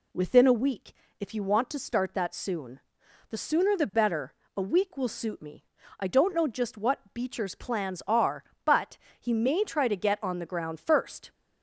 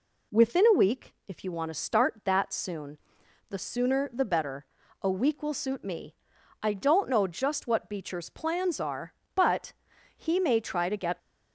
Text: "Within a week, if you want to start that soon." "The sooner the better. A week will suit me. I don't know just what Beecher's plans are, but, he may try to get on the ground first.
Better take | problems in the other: first | stops before "on the ground first"; at 11.1 s

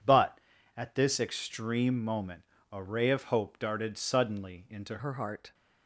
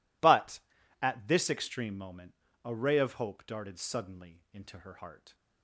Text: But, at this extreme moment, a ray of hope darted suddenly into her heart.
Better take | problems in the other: second | changes voice at "her"; from 4.9 s on; 0.6 s long

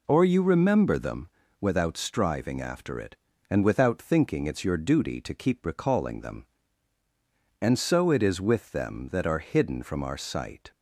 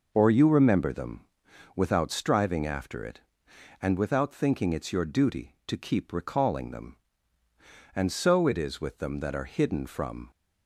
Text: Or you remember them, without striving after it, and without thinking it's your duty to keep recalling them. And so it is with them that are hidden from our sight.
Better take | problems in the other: first | stops before "our sight"; at 10.3 s

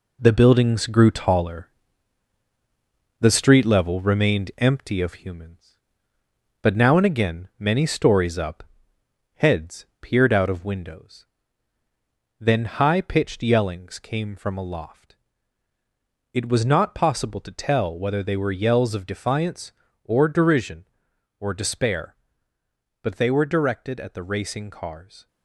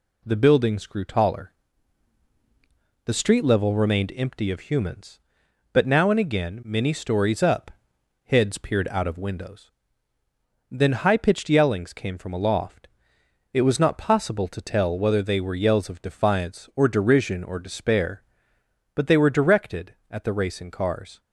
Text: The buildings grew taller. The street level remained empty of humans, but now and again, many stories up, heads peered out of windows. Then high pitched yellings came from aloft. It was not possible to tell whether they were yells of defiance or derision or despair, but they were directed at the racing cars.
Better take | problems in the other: second | gets quieter; noticeable; throughout; 6 dB // pauses between "heads" and "peered"; slight; at 9.8 s; 0.15 s long

